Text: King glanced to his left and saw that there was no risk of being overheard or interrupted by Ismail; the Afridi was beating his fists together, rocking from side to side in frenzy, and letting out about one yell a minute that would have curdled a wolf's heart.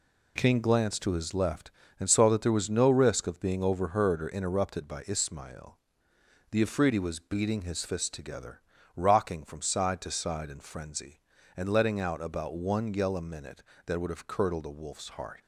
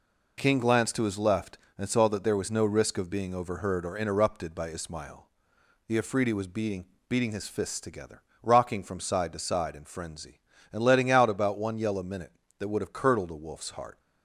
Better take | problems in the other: first | says "beating" twice; at 7.0 s

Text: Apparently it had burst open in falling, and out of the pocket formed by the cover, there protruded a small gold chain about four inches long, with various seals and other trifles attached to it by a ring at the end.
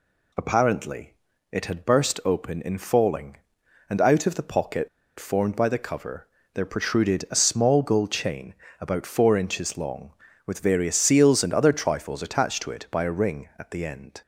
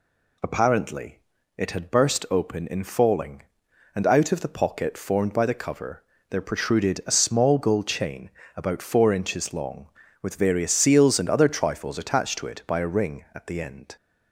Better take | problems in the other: second | pauses between "Apparently" and "it"; at 1.1 s; 0.38 s long; also in the second // pauses between "pocket" and "formed"; slight; at 4.8 s; 0.29 s long // pauses between "chain" and "about"; slight; at 8.5 s; 0.26 s long; slight in the second

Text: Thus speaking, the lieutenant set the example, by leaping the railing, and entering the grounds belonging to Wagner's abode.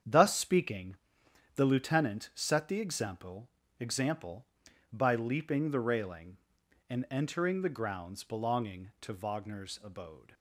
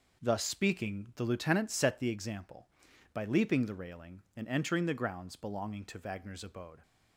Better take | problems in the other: second | starts louder than the rest; strong; until 1.6 s; 8 dB // says "example" twice; at 3.7 s

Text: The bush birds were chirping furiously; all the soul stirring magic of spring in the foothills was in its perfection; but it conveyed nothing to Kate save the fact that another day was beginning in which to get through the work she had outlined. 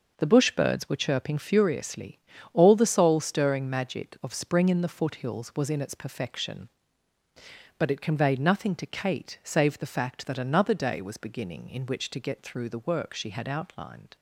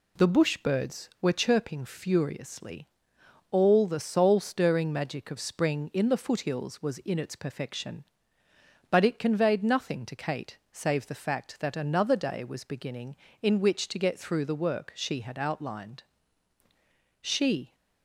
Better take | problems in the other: first | pauses between "Kate" and "save"; slight; at 10.5 s; 0.16 s long // goes on to say "She"; from 17.2 s on; 0.54 s long

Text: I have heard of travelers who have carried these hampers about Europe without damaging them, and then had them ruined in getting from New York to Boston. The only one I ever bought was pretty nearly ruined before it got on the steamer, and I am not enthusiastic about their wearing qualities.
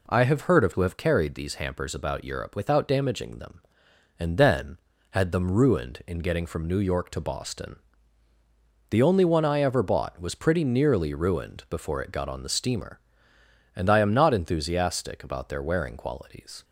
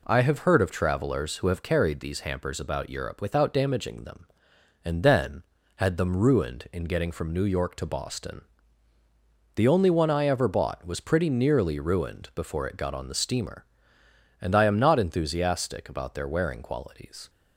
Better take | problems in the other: second | skips "travelers"; at 0.7 s

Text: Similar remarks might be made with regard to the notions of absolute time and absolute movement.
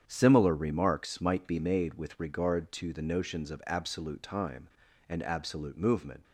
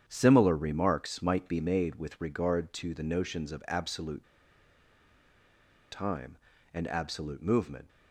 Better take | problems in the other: first | starts louder than the rest; strong; until 1.0 s; 8.5 dB; strong in the first // pauses between "absolute" and "time"; strong; at 4.2 s; 1.6 s long

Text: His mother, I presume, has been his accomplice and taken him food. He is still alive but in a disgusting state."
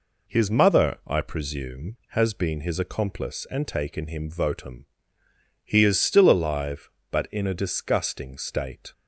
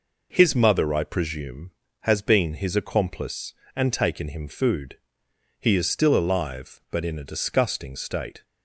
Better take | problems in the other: second | says "votum" for "food"; at 4.2 s

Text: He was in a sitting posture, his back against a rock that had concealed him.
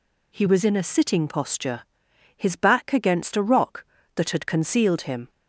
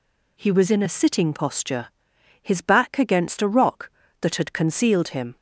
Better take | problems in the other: neither | none

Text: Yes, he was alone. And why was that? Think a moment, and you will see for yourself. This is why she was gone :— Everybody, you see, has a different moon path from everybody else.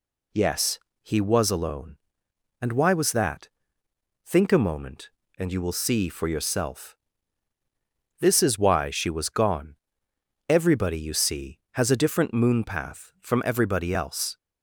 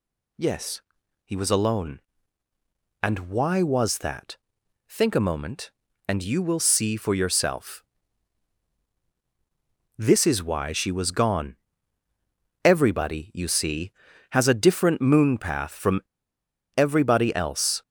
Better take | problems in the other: first | pauses between "from" and "everybody"; noticeable; at 15.9 s; 0.75 s long

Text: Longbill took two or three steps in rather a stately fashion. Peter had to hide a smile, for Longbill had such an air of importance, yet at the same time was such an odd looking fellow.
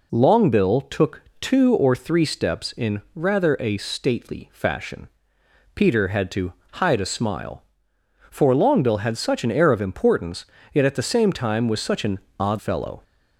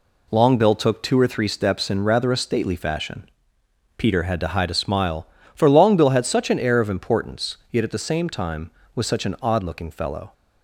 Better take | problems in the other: second | pauses between "took" and "two"; slight; at 1.2 s; 0.18 s long // pauses between "to" and "hide"; slight; at 6.5 s; 0.22 s long // pauses between "an" and "odd"; slight; at 12.1 s; 0.22 s long // skips "looking"; at 12.5 s

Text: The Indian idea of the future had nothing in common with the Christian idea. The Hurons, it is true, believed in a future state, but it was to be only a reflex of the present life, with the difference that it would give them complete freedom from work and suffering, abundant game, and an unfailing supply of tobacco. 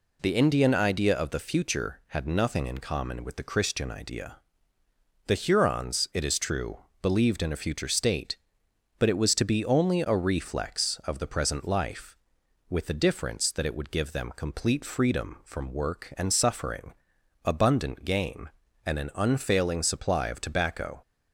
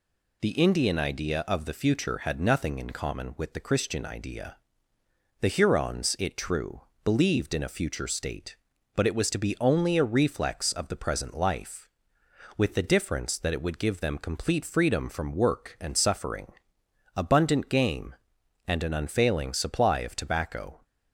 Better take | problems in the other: first | skips "is"; at 6.3 s

